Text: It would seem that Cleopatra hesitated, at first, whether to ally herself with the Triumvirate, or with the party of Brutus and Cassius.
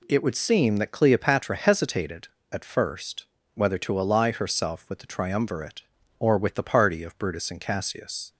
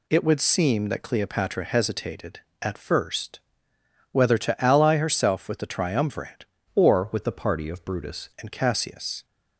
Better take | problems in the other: first | changes voice from "or" to "Brutus"; from 6.7 to 8.2 s; 1.5 s long

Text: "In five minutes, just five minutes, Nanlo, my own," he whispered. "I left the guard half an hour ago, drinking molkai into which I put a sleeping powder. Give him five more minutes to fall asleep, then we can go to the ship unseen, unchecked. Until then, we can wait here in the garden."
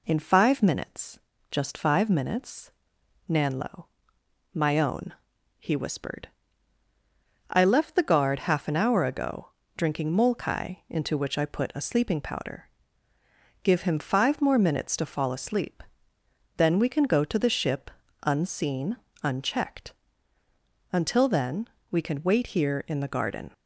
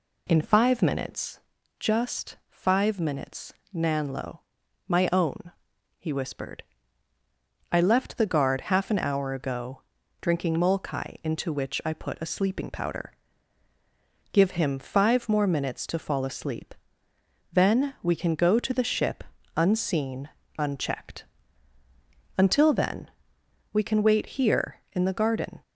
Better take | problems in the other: neither | pauses between "ship" and "unseen"; slight; the same in both

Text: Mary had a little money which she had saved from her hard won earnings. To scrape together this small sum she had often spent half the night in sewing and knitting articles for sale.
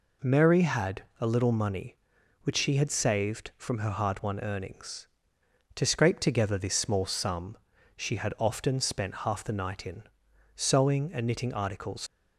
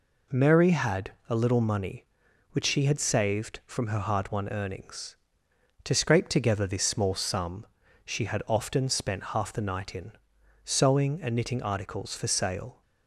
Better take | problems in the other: second | pauses between "had" and "a"; slight; at 1.0 s; 0.18 s long; slight in the second // pauses between "sum" and "she"; at 7.5 s; 0.38 s long; also in the second // pauses between "in" and "sewing"; noticeable; at 10.0 s; 0.54 s long; noticeable in the second // stops before "for sale"; at 12.0 s

